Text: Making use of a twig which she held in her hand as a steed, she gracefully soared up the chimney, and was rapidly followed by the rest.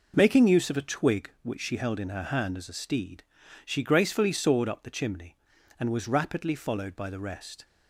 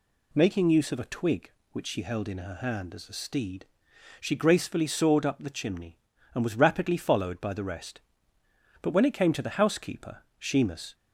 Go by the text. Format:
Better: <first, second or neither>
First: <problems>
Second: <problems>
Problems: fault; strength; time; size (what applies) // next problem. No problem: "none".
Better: first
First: none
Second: goes on to say "But when it came to the housekeeper Shemus"; strong; from 8.8 s on; 2.1 s long